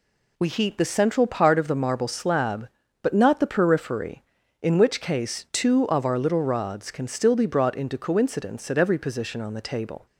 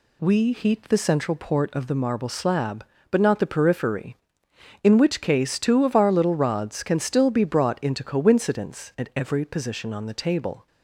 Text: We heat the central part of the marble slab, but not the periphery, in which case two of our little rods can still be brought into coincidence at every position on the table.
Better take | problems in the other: first | says "port" for "part"; at 1.3 s

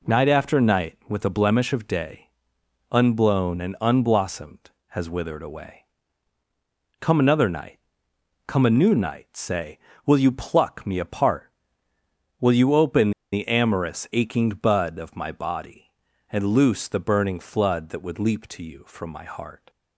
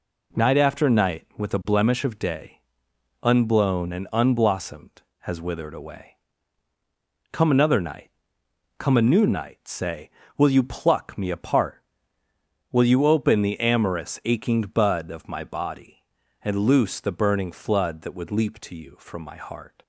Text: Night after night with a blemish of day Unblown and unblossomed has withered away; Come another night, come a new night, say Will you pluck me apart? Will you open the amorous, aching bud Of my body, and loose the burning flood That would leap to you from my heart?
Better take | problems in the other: second | pauses between "day" and "Unblown"; noticeable; at 2.2 s; 0.64 s long; noticeable in the second // pauses between "open" and "the"; slight; at 13.1 s; 0.22 s long

